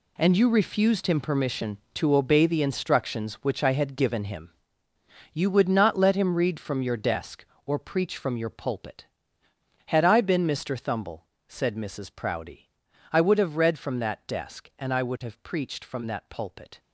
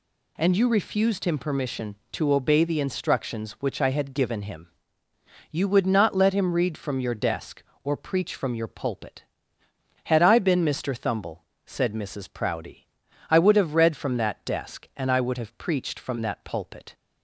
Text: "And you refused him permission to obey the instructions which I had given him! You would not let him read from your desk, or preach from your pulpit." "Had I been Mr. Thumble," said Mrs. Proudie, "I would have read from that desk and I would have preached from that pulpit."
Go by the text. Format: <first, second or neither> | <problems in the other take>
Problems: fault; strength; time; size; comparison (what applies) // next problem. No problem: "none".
second | gets quieter; strong; throughout; 12 dB